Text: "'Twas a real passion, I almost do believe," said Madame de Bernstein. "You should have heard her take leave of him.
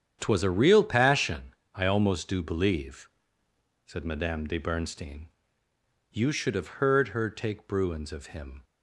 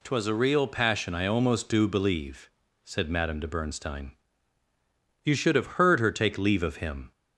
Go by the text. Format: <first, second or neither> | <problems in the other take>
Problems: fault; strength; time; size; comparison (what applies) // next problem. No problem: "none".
second | starts louder than the rest; strong; until 1.2 s; 9 dB // says "bruins" for "leave"; at 7.6 s